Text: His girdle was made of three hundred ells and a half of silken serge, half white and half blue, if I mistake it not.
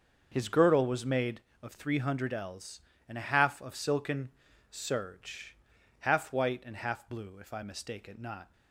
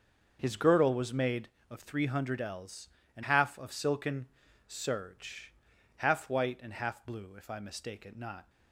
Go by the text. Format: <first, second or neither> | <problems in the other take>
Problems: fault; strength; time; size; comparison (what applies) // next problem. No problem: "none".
first | starts louder than the rest; until 1.4 s; 6.5 dB; also in the first // skips "a"; at 3.2 s // pauses between "silken" and "serge"; at 4.2 s; 0.40 s long; also in the first